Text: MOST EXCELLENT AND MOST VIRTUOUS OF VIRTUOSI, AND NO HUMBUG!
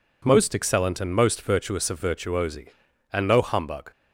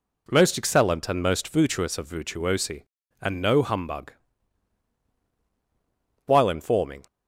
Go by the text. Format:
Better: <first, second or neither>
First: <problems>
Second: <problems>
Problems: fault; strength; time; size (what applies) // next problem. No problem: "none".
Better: first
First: none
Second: goes on to say "While informing"; noticeable; from 6.2 s on; 0.80 s long